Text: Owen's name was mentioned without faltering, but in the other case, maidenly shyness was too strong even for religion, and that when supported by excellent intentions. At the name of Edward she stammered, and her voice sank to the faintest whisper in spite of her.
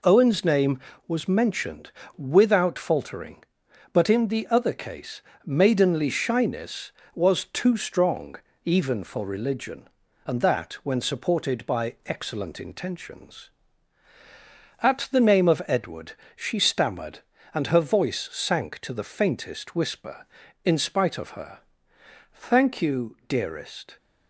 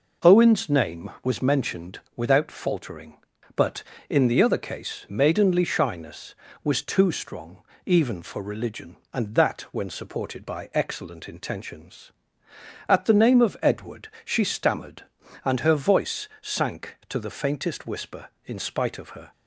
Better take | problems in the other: second | pauses between "mentioned" and "without"; slight; at 1.9 s; 0.26 s long; slight in the second // pauses between "strong" and "even"; slight; at 8.3 s; 0.28 s long; slight in the second // pauses between "Edward" and "she"; slight; at 16.1 s; 0.24 s long; slight in the second // goes on to say "Thank you dearest"; from 22.3 s on; 1.6 s long

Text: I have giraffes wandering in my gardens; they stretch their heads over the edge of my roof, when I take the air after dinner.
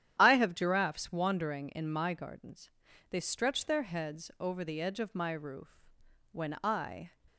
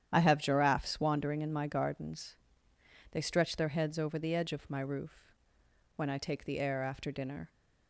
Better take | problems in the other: second | starts louder than the rest; strong; until 1.1 s; 10.5 dB; strong in the second // stops before "take the air after dinner"; at 7.2 s

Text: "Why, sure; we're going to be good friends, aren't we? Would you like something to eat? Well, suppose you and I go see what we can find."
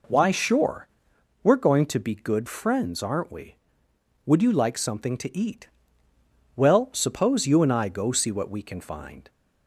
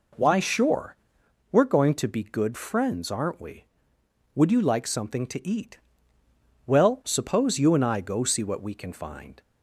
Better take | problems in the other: neither | none

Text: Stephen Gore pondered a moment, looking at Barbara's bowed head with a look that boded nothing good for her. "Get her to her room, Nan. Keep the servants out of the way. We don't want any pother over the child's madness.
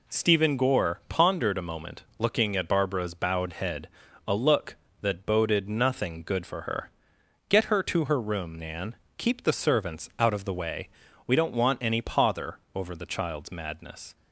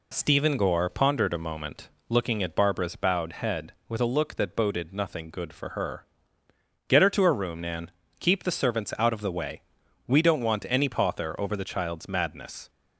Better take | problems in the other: second | skips "with"; at 4.0 s // pauses between "pother" and "over"; slight; at 12.5 s; 0.16 s long

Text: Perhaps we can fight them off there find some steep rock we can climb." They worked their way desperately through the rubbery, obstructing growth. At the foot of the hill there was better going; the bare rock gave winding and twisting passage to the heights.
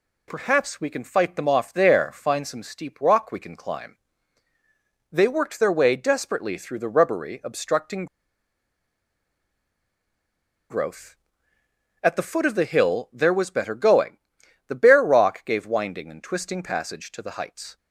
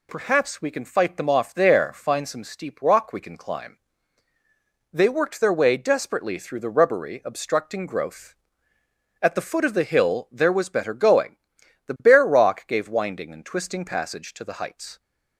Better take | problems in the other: second | pauses between "obstructing" and "growth"; strong; at 8.0 s; 2.6 s long

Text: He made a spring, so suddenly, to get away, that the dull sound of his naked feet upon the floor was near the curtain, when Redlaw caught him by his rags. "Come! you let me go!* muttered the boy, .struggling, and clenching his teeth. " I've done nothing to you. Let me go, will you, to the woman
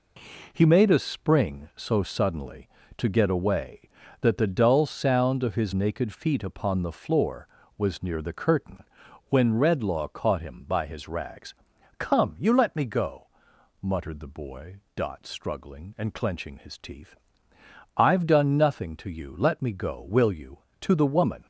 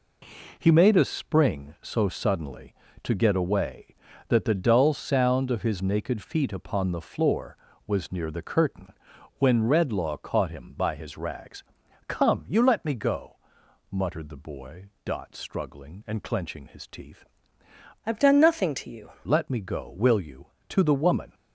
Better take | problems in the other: first | changes voice from "I've" to "you"; from 18.0 to 19.1 s; 1.1 s long

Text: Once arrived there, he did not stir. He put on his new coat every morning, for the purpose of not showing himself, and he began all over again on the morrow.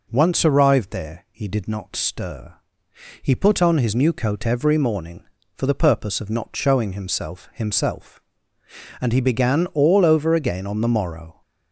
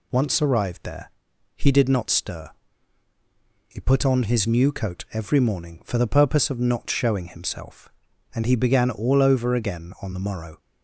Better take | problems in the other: second | says "himself" twice; at 7.5 s

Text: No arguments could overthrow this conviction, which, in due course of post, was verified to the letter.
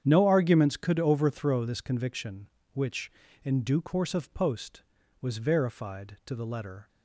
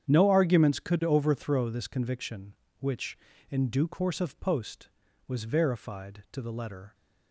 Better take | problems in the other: neither | starts louder than the rest; strong; the same in both

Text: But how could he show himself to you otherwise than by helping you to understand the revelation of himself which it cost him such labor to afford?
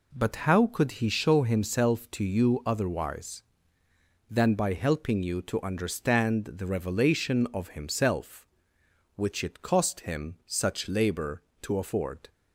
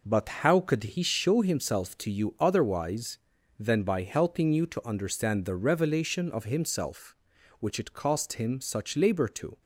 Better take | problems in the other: first | stops before "afford"; at 9.6 s

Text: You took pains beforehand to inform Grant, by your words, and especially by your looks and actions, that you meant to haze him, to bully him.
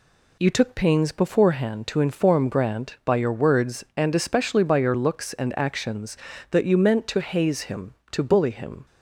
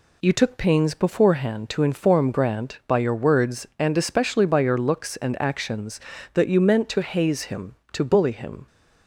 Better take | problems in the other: neither | none

